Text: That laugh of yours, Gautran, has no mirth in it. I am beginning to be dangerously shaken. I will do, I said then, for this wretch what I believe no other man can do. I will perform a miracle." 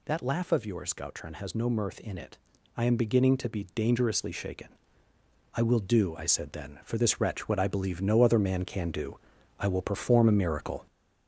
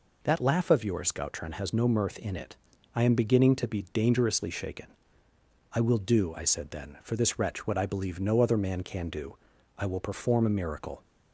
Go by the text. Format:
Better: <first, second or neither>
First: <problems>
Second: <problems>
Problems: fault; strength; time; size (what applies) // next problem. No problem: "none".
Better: second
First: gets louder; noticeable; throughout; 4.5 dB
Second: none